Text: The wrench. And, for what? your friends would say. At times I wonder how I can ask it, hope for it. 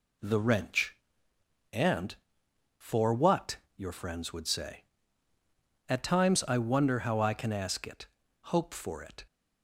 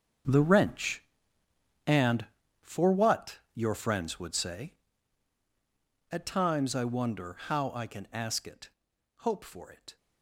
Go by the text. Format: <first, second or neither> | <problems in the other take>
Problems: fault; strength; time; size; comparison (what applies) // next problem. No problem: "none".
first | gets quieter; strong; throughout; 12.5 dB